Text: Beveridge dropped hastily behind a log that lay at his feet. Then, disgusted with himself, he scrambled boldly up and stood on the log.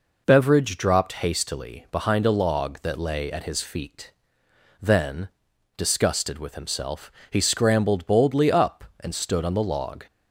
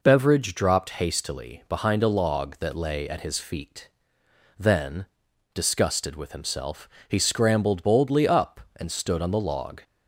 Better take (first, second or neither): neither